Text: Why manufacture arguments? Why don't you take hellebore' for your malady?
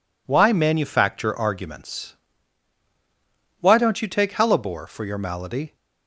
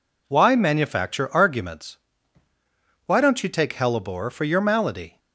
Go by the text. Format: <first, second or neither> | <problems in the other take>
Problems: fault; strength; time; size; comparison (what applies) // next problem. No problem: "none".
neither | none